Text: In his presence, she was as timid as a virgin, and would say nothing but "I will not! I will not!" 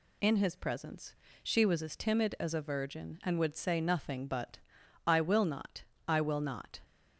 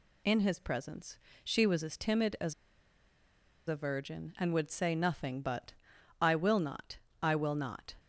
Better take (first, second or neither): first